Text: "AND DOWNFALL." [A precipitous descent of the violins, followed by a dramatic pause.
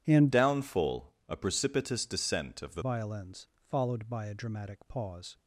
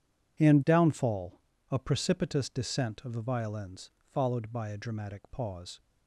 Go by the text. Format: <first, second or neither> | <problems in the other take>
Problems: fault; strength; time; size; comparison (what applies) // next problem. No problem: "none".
second | starts louder than the rest; strong; until 1.0 s; 11 dB // changes voice from "DOWNFALL" to "the"; from 0.3 to 2.8 s; 2.5 s long